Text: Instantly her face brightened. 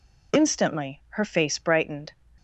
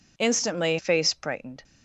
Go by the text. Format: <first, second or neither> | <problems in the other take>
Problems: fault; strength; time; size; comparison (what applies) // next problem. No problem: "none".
first | skips "her"; at 0.7 s